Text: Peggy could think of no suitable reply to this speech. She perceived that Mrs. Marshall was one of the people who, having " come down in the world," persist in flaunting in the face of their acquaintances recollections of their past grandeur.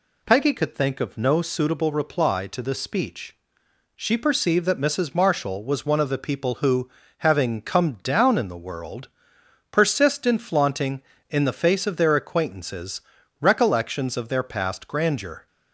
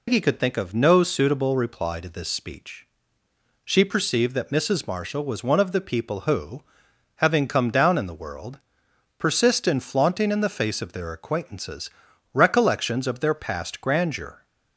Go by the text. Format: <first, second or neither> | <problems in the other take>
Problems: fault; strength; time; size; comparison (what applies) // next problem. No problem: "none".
first | loses the start of "Peggy"; at 0.0 s; 140 ms // pauses between "acquaintances" and "recollections"; at 11.8 s; 0.42 s long; also in the first